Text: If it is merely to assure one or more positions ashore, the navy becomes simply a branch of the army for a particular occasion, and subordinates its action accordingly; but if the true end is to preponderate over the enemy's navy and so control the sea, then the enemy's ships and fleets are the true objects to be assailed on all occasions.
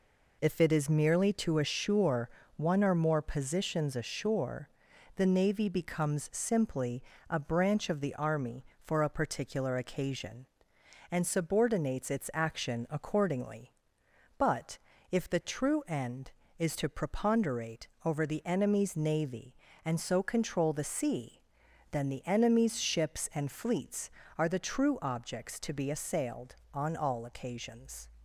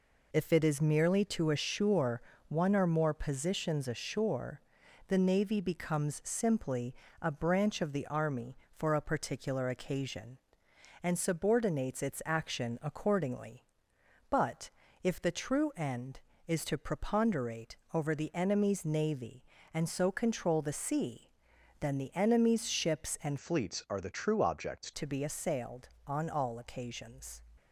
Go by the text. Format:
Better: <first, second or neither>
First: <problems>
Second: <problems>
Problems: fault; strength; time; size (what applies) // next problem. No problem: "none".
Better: first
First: pauses between "assure" and "one"; slight; at 2.2 s; 0.28 s long // pauses between "simply" and "a"; slight; at 7.0 s; 0.28 s long // pauses between "but" and "if"; slight; at 14.7 s; 0.34 s long // pauses between "preponderate" and "over"; slight; at 17.8 s; 0.16 s long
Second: pauses between "assure" and "one"; slight; at 2.2 s; 0.28 s long // pauses between "simply" and "a"; slight; at 6.9 s; 0.28 s long // pauses between "but" and "if"; slight; at 14.6 s; 0.34 s long // pauses between "preponderate" and "over"; slight; at 17.7 s; 0.16 s long // changes voice from "fleets" to "objects"; from 23.3 to 24.9 s; 1.6 s long